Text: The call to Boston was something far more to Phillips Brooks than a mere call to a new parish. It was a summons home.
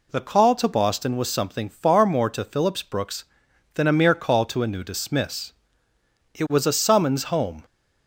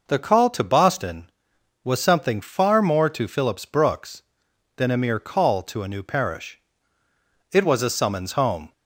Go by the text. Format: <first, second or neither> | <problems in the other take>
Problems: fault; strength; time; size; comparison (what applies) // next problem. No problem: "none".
second | says "dismiss" for "parish"; at 4.8 s